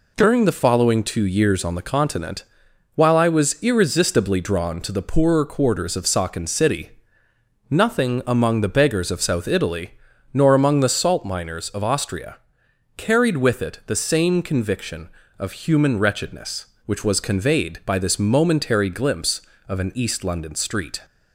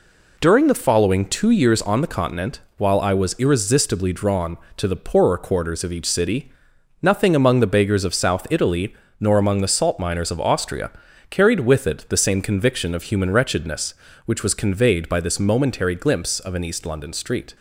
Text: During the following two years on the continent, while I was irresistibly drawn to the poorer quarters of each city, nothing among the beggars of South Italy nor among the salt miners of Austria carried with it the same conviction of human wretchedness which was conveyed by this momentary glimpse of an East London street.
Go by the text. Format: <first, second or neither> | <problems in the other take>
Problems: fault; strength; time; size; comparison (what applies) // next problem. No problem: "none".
second | says "saken" for "each"; at 6.0 s // pauses between "Italy" and "nor"; at 9.9 s; 0.38 s long; slight in the second // pauses between "Austria" and "carried"; noticeable; at 12.3 s; 0.60 s long; also in the second